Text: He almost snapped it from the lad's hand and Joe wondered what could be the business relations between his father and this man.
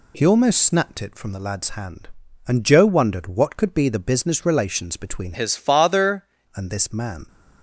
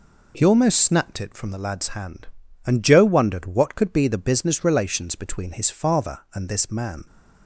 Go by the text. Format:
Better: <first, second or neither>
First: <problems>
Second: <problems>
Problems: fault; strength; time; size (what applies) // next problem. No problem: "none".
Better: second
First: changes voice from "his" to "father"; from 5.3 to 6.2 s; 0.9 s long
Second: none